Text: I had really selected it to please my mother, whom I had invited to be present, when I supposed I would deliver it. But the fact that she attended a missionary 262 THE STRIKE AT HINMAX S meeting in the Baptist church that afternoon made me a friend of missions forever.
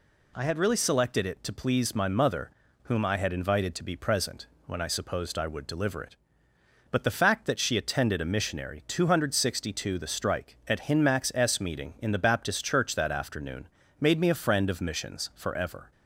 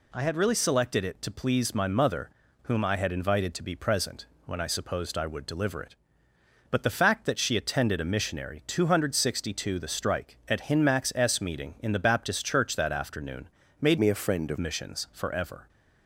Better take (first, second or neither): first